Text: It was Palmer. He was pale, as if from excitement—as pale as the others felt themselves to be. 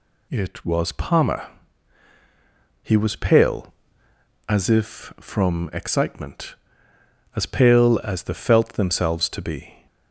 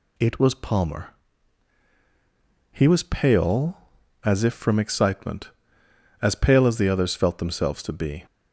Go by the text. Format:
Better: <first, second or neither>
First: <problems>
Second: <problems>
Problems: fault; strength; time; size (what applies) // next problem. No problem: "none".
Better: second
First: skips "others"; at 8.3 s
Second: none